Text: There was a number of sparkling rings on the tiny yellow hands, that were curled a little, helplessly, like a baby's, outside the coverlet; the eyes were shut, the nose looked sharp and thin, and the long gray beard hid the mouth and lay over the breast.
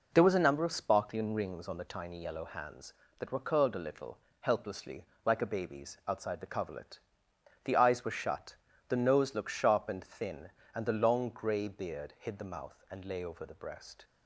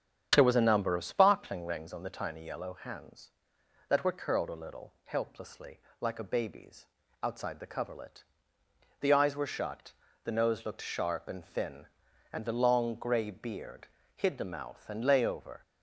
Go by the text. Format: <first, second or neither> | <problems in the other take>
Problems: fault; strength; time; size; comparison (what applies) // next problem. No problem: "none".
first | starts louder than the rest; strong; until 1.3 s; 8.5 dB // pauses between "beard" and "hid"; slight; at 13.8 s; 0.30 s long // stops before "the breast"; at 15.6 s